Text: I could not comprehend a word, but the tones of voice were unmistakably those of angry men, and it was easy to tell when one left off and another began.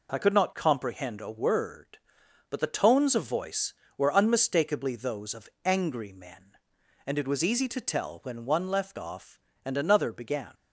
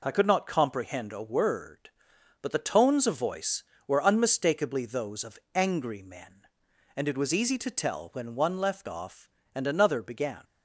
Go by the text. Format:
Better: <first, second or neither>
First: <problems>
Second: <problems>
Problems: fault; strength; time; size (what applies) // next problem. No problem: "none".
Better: neither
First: pauses between "of" and "angry"; slight; at 5.4 s; 0.16 s long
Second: pauses between "of" and "angry"; slight; at 5.3 s; 0.16 s long